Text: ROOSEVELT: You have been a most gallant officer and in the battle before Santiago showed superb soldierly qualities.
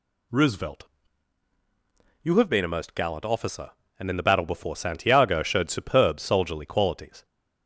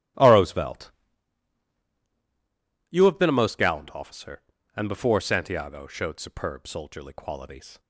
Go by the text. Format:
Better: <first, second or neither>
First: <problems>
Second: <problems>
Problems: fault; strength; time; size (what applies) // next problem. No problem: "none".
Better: first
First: none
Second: starts louder than the rest; strong; until 3.1 s; 15.5 dB // skips "in the battle"; at 4.8 s